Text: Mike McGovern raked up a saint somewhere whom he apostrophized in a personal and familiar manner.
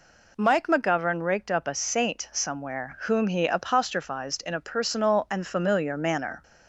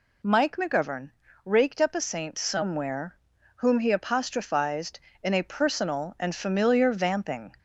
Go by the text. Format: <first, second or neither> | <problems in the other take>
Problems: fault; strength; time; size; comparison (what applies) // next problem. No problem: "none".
first | pauses between "McGovern" and "raked"; slight; at 1.1 s; 0.34 s long // pauses between "somewhere" and "whom"; at 3.1 s; 0.40 s long // says "vamping" for "manner"; at 6.9 s